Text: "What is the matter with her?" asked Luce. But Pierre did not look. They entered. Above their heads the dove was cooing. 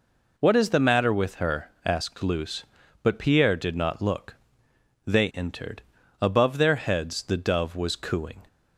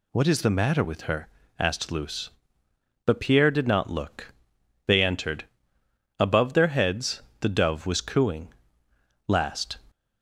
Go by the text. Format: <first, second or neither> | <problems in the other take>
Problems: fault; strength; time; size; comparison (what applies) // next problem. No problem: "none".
first | pauses between "heads" and "the"; slight; at 7.2 s; 0.20 s long // goes on to say "Last"; from 9.2 s on; 0.52 s long